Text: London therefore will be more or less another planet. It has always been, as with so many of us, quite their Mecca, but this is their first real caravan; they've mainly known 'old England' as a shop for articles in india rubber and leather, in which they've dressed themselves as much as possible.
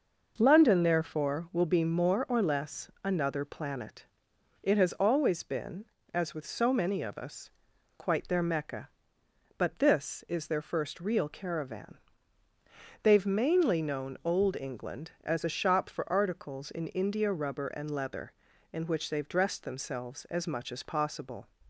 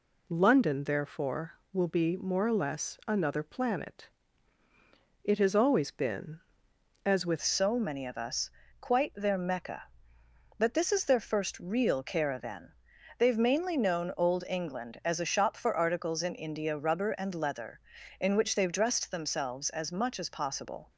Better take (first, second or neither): first